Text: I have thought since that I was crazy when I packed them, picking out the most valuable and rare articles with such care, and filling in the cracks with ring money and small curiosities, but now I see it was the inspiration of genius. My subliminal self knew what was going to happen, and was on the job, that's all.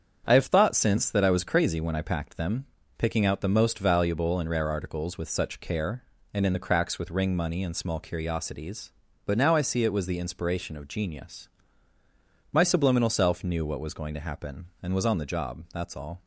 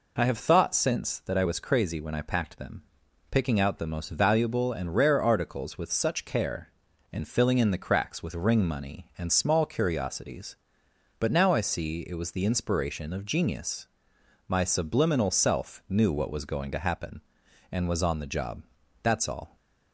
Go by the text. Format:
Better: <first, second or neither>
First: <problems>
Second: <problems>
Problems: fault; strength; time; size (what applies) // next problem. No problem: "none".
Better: second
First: starts louder than the rest; strong; until 1.3 s; 8 dB // skips "filling"; at 6.4 s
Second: none